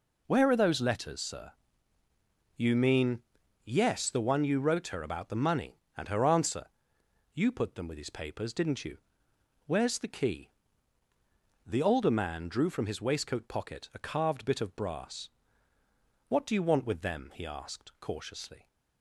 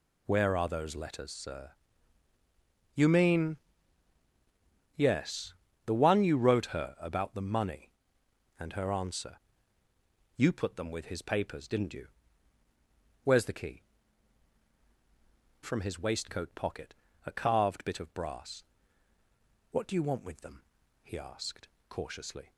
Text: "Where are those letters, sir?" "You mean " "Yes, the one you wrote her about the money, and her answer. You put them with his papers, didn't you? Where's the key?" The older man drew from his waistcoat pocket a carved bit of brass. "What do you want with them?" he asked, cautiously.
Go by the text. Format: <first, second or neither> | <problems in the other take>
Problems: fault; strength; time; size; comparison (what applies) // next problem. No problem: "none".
first | skips "The older man drew"; at 14.7 s // pauses between "pocket" and "a"; slight; at 16.9 s; 0.32 s long